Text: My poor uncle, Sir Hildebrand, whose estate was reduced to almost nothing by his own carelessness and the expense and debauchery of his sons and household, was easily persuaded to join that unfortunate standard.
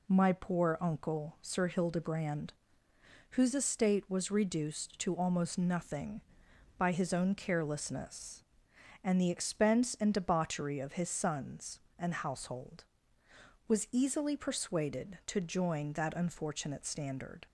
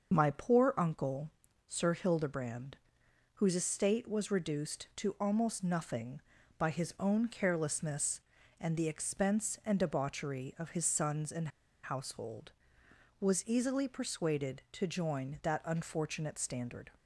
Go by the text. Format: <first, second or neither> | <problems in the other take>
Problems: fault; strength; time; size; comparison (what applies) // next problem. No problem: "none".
first | starts louder than the rest; until 1.1 s; 6.5 dB // pauses between "and" and "household"; slight; at 11.4 s; 0.34 s long